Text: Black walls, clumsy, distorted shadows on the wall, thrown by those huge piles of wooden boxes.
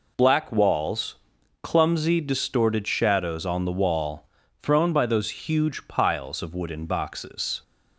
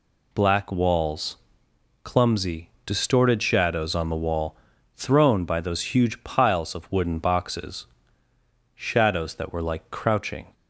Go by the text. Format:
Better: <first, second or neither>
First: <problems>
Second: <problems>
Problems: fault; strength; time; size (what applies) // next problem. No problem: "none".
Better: first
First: none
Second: goes on to say "Shadows that were like crouching"; strong; from 8.7 s on; 1.8 s long